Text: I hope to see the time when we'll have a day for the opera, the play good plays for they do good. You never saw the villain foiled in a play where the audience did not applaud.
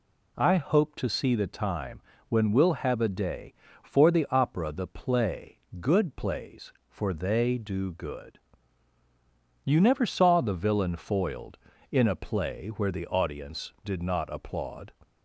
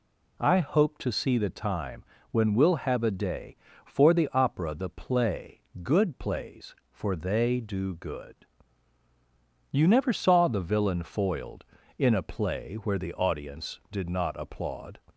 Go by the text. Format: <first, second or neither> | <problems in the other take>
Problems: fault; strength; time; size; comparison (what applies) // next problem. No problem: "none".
neither | pauses between "time" and "when"; slight; the same in both // pauses between "play" and "good"; slight; the same in both